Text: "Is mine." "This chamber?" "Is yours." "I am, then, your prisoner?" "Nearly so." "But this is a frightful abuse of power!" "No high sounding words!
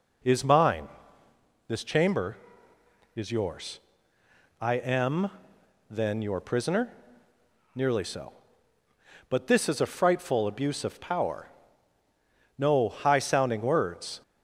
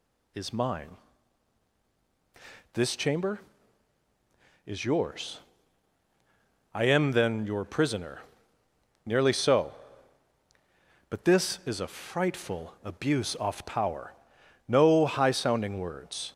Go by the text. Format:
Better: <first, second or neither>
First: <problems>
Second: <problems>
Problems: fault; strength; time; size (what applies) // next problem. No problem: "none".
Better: first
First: none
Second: says "off" for "of"; at 13.3 s